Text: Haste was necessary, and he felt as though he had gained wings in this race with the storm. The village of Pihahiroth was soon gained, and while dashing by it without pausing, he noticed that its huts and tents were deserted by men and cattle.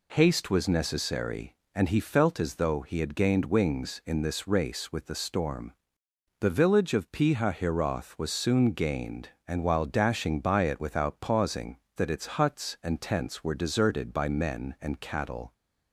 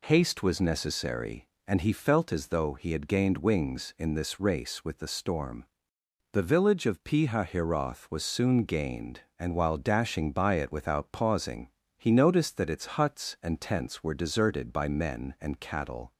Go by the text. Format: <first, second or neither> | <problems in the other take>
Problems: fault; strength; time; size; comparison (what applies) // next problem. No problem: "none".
second | skips "he noticed"; at 11.8 s